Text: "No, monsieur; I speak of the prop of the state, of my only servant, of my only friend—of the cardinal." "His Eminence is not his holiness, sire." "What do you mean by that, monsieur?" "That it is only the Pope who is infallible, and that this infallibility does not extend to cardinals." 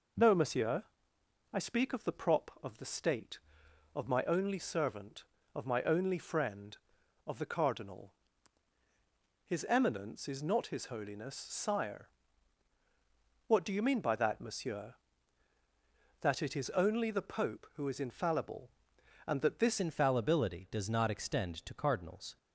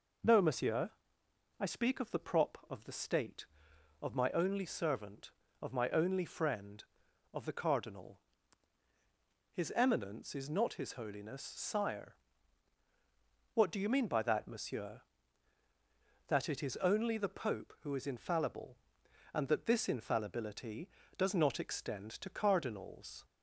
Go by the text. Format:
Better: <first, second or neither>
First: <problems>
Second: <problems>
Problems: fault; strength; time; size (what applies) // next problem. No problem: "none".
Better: second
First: changes voice at "infallibility"; from 19.7 s on; 2.6 s long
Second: none